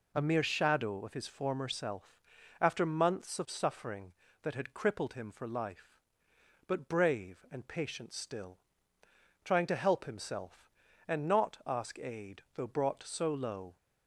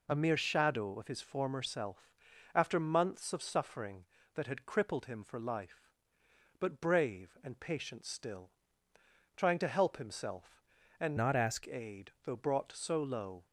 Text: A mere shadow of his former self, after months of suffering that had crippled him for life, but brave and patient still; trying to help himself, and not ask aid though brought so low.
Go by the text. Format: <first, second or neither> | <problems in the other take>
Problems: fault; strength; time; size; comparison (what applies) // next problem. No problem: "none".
first | changes voice from "not" to "ask"; from 11.1 to 11.6 s; 0.5 s long